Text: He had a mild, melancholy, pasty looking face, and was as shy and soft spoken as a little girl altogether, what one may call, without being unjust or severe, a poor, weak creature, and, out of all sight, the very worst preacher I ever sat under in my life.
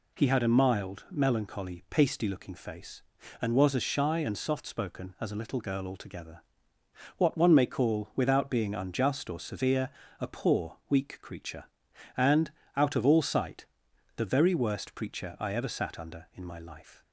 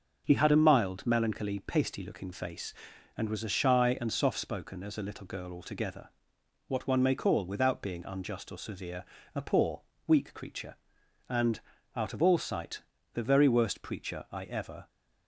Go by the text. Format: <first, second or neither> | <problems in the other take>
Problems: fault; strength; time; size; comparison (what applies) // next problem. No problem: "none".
first | starts louder than the rest; noticeable; until 1.2 s; 6 dB // stops before "sat under in my life"; at 14.8 s